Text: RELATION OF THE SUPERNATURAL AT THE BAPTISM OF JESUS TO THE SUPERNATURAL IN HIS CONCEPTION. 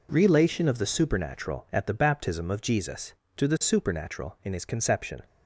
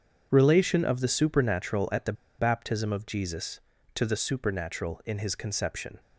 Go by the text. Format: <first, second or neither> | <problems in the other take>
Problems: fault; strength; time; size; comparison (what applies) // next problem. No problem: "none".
first | starts louder than the rest; strong; until 1.3 s; 7.5 dB // pauses between "THE" and "BAPTISM"; slight; at 2.1 s; 0.26 s long